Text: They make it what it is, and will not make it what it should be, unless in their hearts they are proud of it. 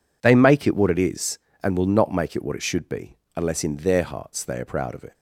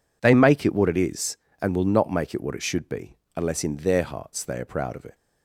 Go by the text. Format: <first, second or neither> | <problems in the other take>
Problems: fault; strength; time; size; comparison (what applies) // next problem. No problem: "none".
neither | none